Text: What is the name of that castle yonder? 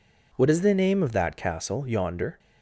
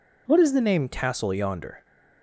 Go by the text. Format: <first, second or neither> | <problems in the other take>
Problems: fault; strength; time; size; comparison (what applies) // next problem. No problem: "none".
first | skips "of that"; at 0.8 s